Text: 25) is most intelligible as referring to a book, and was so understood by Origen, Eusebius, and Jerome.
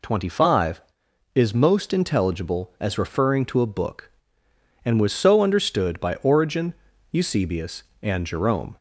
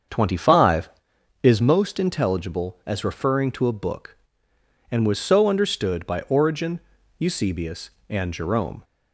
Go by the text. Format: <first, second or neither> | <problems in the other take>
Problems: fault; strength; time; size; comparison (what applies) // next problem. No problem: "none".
first | starts louder than the rest; until 1.7 s; 7 dB